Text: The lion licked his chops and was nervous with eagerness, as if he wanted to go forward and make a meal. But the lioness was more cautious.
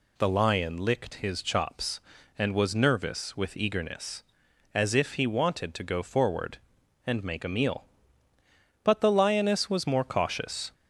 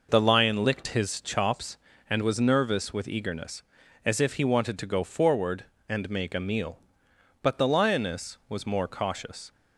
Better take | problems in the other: neither | none

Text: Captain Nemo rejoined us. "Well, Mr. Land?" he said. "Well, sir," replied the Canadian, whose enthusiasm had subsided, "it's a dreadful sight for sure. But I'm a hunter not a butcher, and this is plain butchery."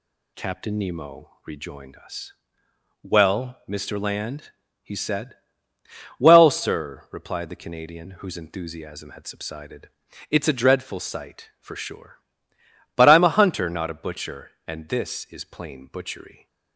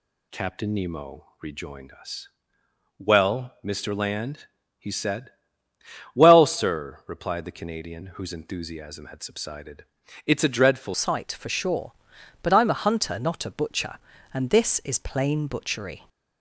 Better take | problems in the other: first | changes voice at "sight"; from 10.9 s on; 5.1 s long

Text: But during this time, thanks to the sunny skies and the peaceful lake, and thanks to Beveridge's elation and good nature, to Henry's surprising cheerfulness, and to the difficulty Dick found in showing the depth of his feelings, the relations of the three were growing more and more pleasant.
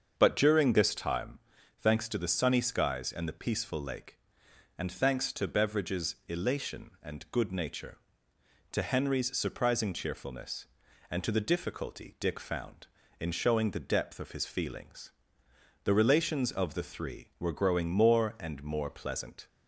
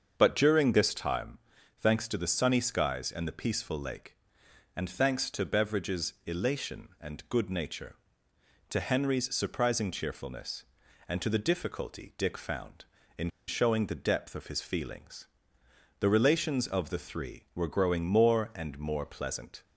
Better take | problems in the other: first | starts louder than the rest; until 1.1 s; 7 dB; also in the first // pauses between "in" and "showing"; slight; at 13.2 s; 0.19 s long

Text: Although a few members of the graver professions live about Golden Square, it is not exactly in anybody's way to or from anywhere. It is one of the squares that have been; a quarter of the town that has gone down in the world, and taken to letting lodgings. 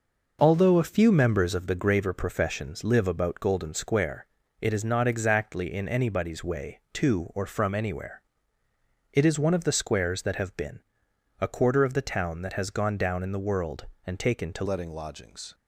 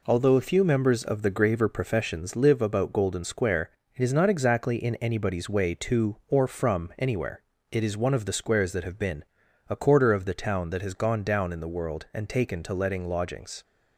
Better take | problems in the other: second | changes voice at "letting"; from 14.6 s on; 0.9 s long

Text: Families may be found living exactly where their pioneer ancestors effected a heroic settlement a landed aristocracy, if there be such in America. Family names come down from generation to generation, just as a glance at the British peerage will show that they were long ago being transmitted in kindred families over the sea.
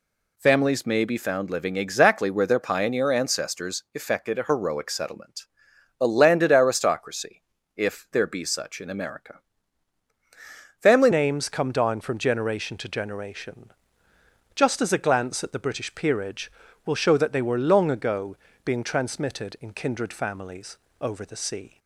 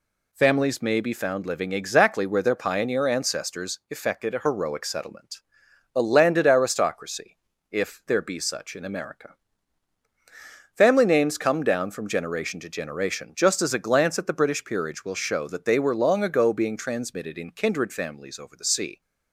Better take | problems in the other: second | pauses between "settlement" and "a"; noticeable; at 5.4 s; 0.56 s long; noticeable in the second // changes voice at "names"; from 11.1 s on; 10.6 s long // pauses between "ago" and "being"; slight; at 18.3 s; 0.28 s long // pauses between "families" and "over"; slight; at 20.7 s; 0.24 s long

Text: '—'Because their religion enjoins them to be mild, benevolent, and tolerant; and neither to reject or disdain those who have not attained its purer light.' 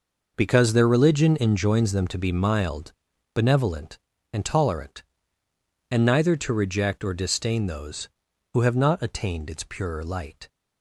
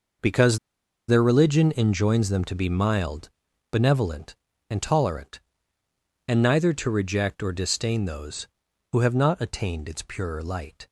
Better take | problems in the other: first | pauses between "Because" and "their"; noticeable; at 0.5 s; 0.49 s long

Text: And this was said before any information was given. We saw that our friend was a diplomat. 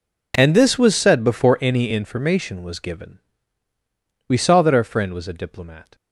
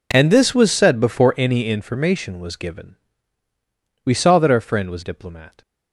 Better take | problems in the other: first | skips "a"; at 5.0 s

